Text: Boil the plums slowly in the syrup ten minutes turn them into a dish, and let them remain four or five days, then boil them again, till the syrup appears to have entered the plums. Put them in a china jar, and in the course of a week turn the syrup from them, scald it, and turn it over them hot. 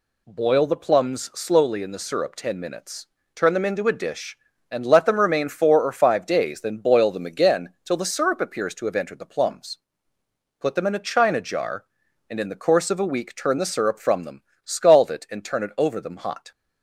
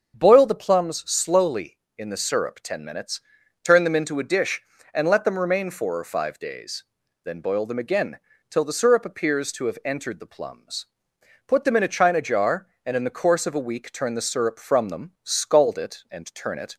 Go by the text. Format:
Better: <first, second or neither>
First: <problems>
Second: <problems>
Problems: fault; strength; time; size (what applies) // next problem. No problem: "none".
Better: first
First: pauses between "minutes" and "turn"; slight; at 3.0 s; 0.26 s long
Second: starts louder than the rest; until 1.1 s; 7 dB // pauses between "minutes" and "turn"; at 3.2 s; 0.44 s long // stops before "over them hot"; at 16.7 s